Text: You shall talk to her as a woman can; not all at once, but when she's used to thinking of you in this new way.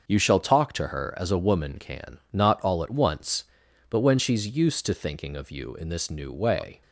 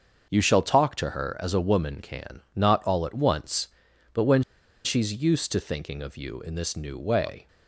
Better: first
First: starts louder than the rest; until 1.1 s; 6.5 dB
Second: starts louder than the rest; until 1.3 s; 6.5 dB // pauses between "when" and "she's"; at 4.4 s; 0.42 s long

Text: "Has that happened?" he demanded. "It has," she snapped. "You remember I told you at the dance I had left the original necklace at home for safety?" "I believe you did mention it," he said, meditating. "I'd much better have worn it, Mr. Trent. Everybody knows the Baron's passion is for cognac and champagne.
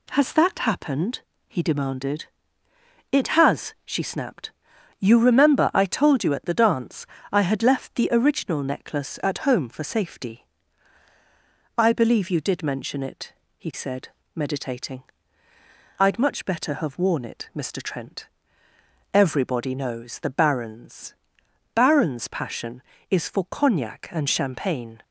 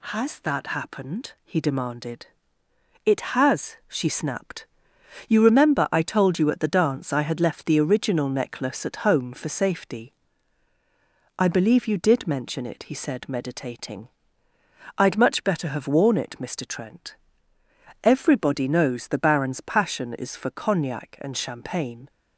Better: second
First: pauses between "dance" and "I"; slight; at 7.0 s; 0.24 s long // says "Baron's" twice; at 21.7 s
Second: none

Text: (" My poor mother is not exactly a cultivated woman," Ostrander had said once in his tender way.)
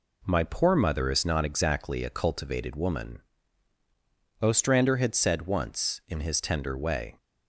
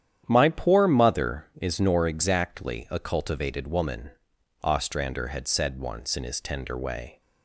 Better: first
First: none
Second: starts louder than the rest; strong; until 1.2 s; 9.5 dB // says "nor" for "not"; at 1.7 s

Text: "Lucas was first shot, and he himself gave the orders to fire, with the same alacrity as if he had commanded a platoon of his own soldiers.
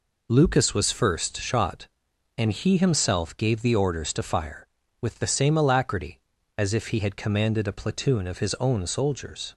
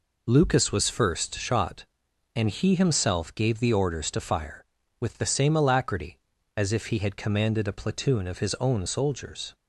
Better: neither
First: none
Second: none

